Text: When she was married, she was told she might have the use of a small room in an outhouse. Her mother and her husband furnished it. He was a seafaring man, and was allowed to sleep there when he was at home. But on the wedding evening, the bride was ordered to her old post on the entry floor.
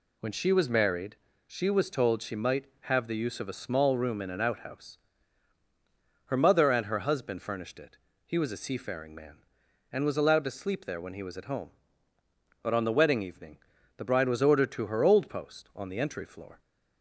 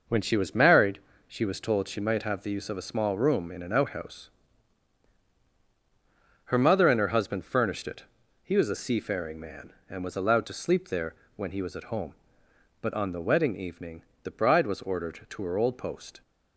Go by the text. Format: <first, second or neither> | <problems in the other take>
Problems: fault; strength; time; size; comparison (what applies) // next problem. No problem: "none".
first | pauses between "there" and "when"; slight; at 11.1 s; 0.22 s long // stops before "on the entry floor"; at 16.2 s